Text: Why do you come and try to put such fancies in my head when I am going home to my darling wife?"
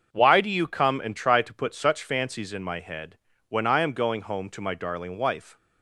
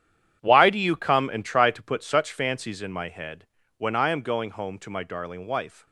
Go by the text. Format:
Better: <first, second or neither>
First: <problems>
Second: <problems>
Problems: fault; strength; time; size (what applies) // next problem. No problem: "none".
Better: first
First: starts louder than the rest; until 1.1 s; 6.5 dB // pauses between "head" and "when"; slight; at 3.1 s; 0.32 s long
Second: gets quieter; strong; throughout; 12.5 dB // starts louder than the rest; strong; until 1.4 s; 9.5 dB // pauses between "head" and "when"; slight; at 3.4 s; 0.32 s long